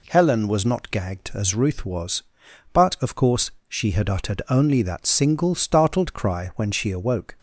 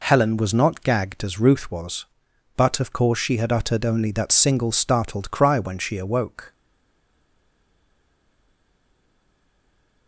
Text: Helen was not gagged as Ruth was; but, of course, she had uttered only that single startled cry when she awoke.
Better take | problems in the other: first | stays silent after the last word; strong; from 6.5 s on; 3.5 s long

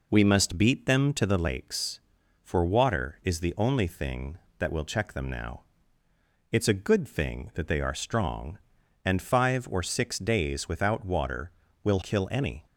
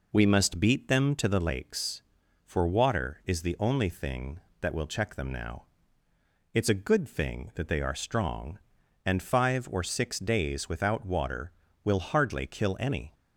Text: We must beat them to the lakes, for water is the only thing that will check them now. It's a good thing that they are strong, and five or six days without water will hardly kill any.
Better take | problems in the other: second | skips "hardly"; at 12.0 s

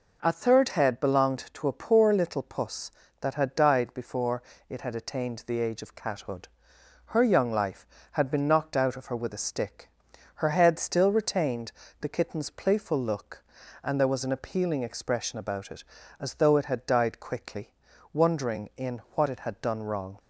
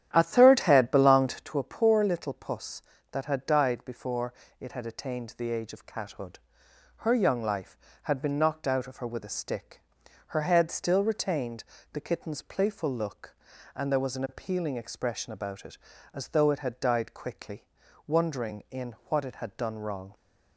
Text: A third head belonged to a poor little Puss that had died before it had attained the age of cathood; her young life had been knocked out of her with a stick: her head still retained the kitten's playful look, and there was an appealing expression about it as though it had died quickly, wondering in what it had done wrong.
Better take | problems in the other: first | starts louder than the rest; strong; until 1.6 s; 10.5 dB // pauses between "before" and "it"; slight; at 4.3 s; 0.26 s long; slight in the first // pauses between "retained" and "the"; slight; at 11.6 s; 0.30 s long; slight in the first // pauses between "in" and "what"; slight; at 18.9 s; 0.16 s long; slight in the first

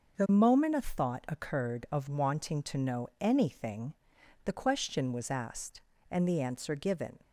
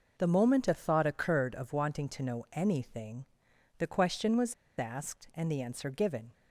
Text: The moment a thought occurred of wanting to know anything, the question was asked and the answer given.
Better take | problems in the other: first | pauses between "was" and "asked"; slight; at 4.5 s; 0.23 s long

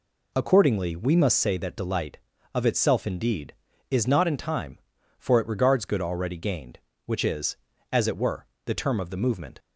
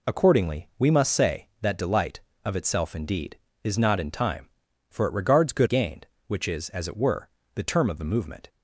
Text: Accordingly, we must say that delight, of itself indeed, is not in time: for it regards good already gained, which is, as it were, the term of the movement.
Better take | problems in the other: first | skips "already"; at 5.6 s

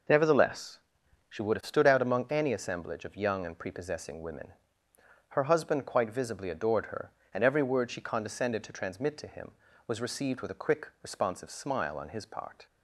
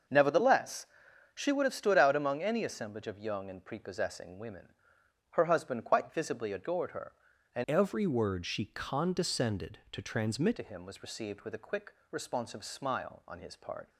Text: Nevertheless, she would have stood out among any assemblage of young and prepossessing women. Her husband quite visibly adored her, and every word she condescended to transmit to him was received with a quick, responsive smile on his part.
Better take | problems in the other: first | starts louder than the rest; until 1.5 s; 6.5 dB // changes voice from "every" to "transmit"; from 7.6 to 10.5 s; 2.9 s long

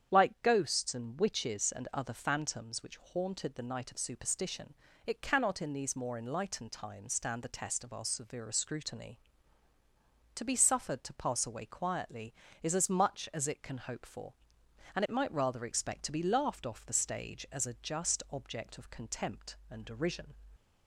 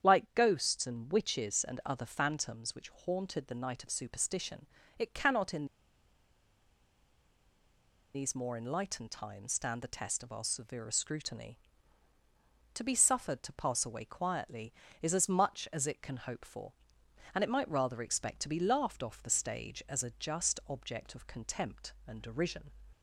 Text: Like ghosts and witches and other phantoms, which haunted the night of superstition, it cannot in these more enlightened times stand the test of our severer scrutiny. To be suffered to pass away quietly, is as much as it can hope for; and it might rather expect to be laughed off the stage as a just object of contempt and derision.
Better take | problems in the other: first | starts louder than the rest; strong; until 1.1 s; 8.5 dB; strong in the first // pauses between "in" and "these"; strong; at 5.6 s; 2.4 s long

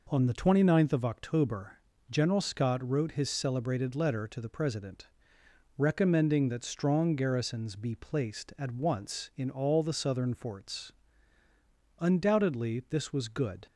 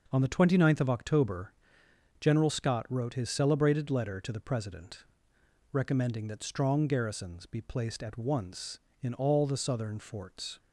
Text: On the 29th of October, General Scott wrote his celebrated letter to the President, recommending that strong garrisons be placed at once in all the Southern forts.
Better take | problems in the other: second | goes on to say "Undoubtedly this was good"; strong; from 11.9 s on; 1.6 s long

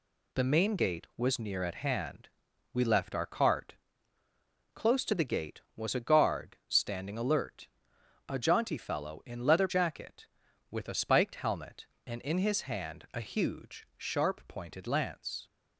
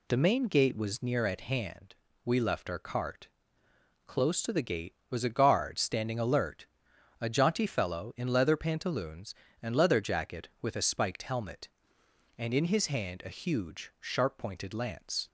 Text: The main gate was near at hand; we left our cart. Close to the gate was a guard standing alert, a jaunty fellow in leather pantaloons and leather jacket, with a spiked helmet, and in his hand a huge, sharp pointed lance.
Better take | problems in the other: second | skips "pantaloons and leather"; at 9.6 s

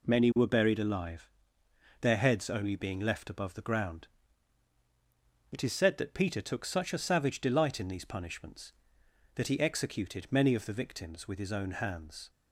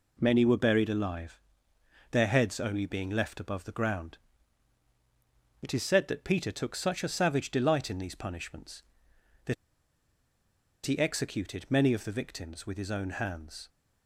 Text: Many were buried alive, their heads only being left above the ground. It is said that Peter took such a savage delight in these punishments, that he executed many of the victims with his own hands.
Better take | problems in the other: first | pauses between "that" and "he"; strong; at 9.5 s; 1.3 s long

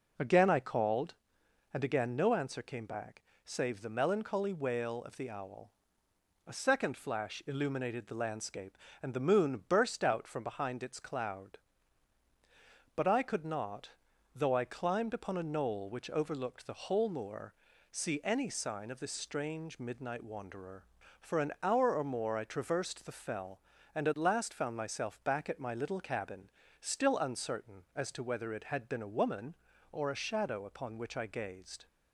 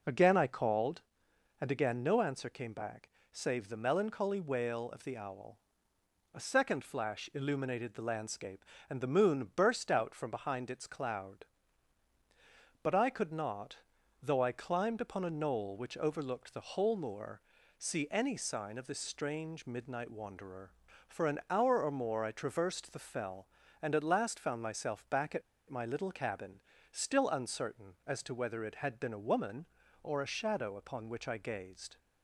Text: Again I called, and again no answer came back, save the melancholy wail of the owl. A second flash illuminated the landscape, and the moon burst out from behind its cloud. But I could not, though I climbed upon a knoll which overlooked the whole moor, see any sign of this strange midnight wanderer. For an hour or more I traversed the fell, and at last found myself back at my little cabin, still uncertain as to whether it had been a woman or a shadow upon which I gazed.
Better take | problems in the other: first | pauses between "at" and "my"; slight; at 25.4 s; 0.28 s long

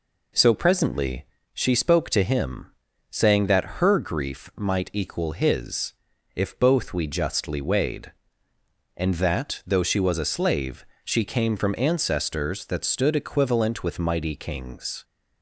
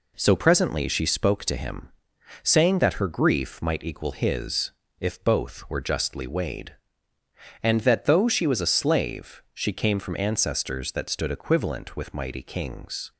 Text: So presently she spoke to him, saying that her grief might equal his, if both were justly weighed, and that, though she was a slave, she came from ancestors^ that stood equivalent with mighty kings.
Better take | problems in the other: second | pauses between "presently" and "she"; slight; at 1.2 s; 0.28 s long // says "we" for "were"; at 6.9 s

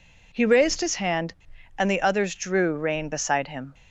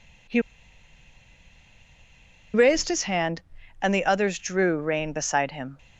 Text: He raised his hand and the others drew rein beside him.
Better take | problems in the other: first | pauses between "He" and "raised"; strong; at 0.4 s; 2.1 s long

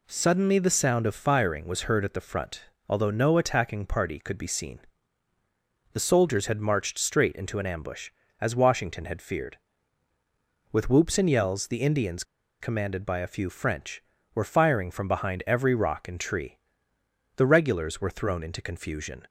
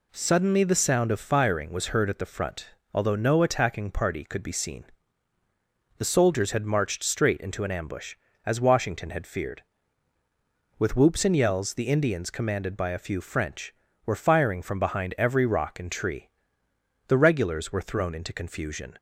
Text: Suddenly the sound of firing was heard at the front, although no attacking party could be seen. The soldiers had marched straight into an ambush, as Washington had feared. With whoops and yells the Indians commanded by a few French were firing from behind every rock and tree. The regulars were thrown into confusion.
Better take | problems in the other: second | pauses between "Indians" and "commanded"; at 12.2 s; 0.36 s long

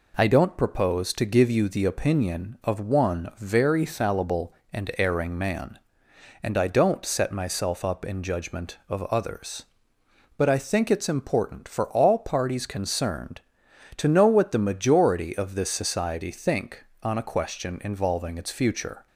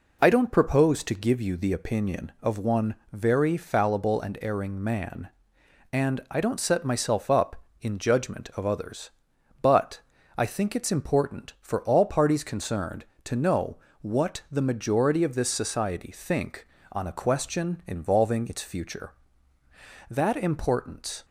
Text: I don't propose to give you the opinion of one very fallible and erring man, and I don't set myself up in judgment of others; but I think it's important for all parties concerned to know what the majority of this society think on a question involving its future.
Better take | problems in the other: first | pauses between "one" and "very"; slight; at 2.9 s; 0.16 s long // pauses between "but" and "I"; slight; at 10.0 s; 0.34 s long // pauses between "know" and "what"; slight; at 13.7 s; 0.24 s long // goes on to say "That importance"; noticeable; from 20.0 s on; 1.1 s long

